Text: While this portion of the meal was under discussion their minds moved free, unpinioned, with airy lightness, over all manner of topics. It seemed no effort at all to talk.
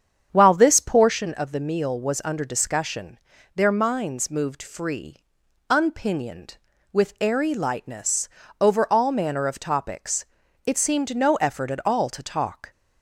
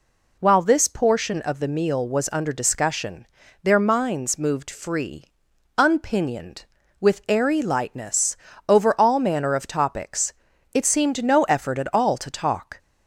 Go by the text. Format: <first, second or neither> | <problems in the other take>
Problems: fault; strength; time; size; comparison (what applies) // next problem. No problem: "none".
second | starts louder than the rest; strong; until 1.2 s; 8 dB // pauses between "discussion" and "their"; at 3.1 s; 0.38 s long; also in the second